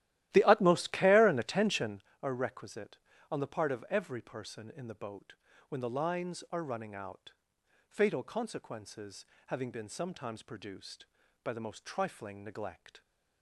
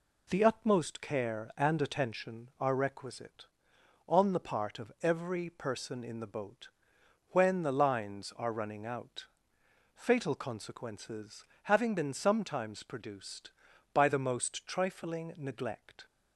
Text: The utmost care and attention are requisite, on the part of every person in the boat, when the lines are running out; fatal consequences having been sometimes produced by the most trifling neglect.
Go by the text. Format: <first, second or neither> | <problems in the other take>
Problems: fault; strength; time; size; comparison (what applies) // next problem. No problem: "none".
second | starts louder than the rest; strong; until 2.1 s; 14 dB // pauses between "consequences" and "having"; slight; at 9.2 s; 0.22 s long; slight in the second